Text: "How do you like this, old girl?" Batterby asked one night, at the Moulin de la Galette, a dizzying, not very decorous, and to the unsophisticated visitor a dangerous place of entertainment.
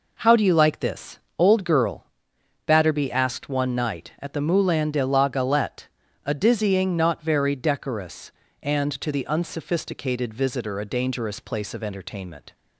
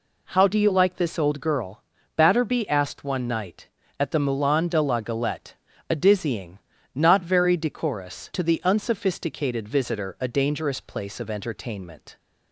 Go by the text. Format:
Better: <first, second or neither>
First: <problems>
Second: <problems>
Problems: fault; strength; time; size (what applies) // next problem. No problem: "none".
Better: first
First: none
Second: skips "and"; at 8.3 s